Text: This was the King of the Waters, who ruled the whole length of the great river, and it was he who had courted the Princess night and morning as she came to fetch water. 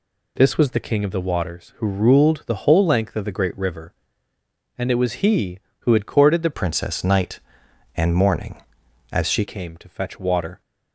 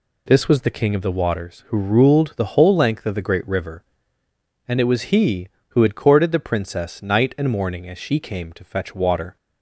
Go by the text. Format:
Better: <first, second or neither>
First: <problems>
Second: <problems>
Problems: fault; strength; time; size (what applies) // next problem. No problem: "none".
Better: second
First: changes voice from "Princess" to "she"; from 6.5 to 9.4 s; 2.9 s long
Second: none